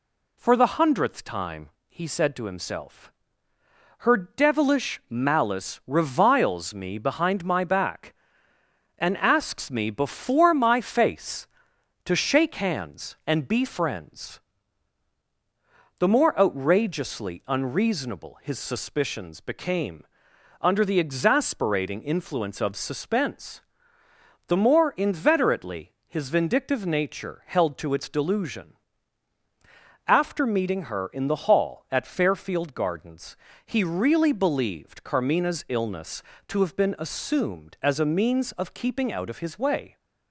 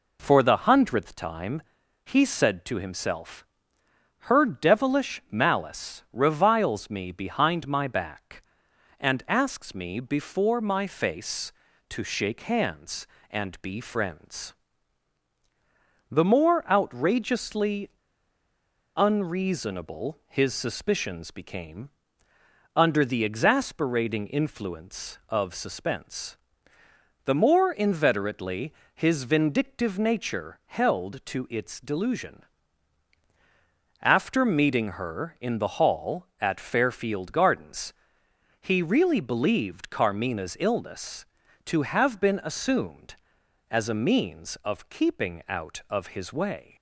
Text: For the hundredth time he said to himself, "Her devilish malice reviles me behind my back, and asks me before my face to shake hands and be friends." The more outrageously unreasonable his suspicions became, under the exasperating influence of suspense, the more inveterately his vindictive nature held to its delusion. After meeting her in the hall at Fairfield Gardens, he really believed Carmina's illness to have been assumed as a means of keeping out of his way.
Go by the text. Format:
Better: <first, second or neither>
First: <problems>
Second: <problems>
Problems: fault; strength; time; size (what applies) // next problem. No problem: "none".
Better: first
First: pauses between "time" and "he"; slight; at 1.7 s; 0.18 s long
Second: pauses between "time" and "he"; at 1.6 s; 0.42 s long // pauses between "outrageously" and "unreasonable"; at 17.8 s; 1.0 s long // pauses between "inveterately" and "his"; slight; at 28.7 s; 0.24 s long